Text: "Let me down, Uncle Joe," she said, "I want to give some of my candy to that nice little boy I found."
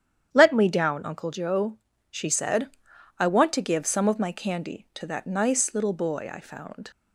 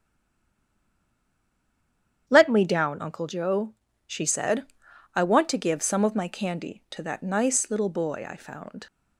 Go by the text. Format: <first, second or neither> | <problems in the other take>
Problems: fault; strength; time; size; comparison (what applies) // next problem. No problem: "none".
first | stays silent before the first word; until 2.2 s; 2.2 s long // starts louder than the rest; strong; until 3.2 s; 9.5 dB; strong in the first